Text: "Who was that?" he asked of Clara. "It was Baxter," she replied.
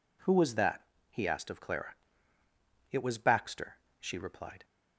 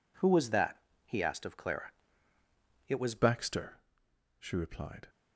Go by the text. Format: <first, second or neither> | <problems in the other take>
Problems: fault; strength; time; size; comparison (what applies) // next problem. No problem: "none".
first | changes voice at "Baxter"; from 3.1 s on; 1.9 s long